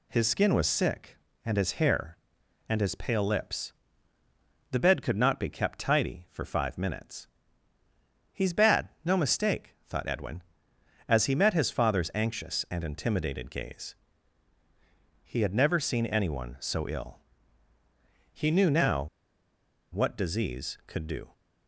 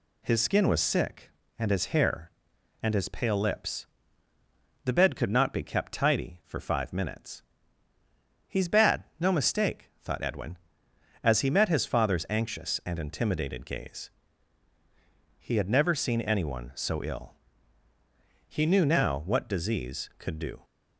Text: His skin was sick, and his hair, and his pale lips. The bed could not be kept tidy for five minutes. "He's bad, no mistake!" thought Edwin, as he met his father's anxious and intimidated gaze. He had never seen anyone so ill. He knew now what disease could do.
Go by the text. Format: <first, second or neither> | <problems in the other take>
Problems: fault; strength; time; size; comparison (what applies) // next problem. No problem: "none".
second | pauses between "now" and "what"; noticeable; at 19.0 s; 0.91 s long